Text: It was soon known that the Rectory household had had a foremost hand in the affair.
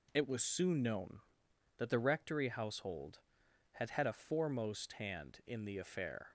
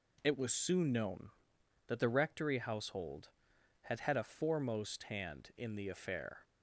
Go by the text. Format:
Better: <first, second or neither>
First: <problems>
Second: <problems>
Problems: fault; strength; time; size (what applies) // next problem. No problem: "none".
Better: neither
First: none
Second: none